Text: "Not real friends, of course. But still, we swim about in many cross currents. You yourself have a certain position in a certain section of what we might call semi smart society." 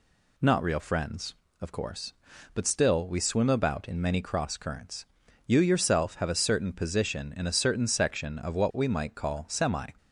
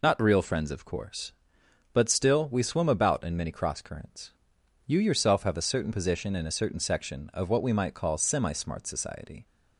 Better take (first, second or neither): second